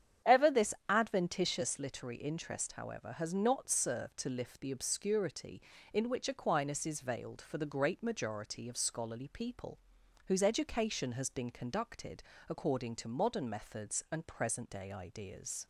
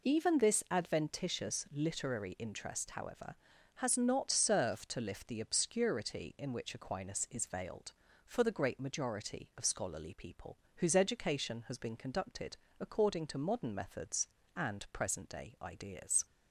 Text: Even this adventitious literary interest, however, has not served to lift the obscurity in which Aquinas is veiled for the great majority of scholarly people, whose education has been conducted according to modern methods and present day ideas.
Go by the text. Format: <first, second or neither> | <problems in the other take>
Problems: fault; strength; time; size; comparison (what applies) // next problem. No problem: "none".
second | starts louder than the rest; strong; until 1.4 s; 9 dB // says "Ever" for "Even"; at 0.2 s // pauses between "this" and "adventitious"; slight; at 0.7 s; 0.16 s long // pauses between "conducted" and "according"; slight; at 12.2 s; 0.26 s long; slight in the second